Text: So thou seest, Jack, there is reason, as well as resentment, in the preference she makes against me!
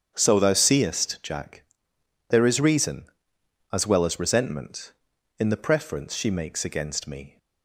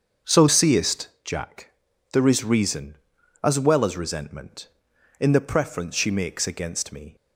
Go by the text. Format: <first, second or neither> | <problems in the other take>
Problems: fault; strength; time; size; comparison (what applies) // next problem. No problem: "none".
first | starts louder than the rest; until 1.4 s; 7 dB; strong in the first // skips "thou"; at 0.4 s